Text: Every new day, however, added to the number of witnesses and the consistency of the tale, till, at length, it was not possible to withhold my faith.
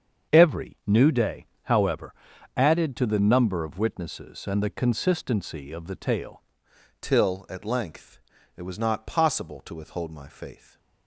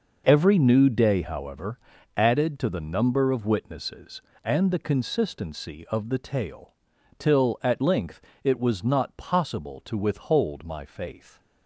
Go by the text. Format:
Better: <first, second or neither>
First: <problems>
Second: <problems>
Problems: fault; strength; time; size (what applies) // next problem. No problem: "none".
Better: second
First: starts louder than the rest; until 1.3 s; 7 dB // changes voice at "till"; from 7.0 s on; 3.7 s long // stays silent after the last word; slight; from 10.5 s on; 0.5 s long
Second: none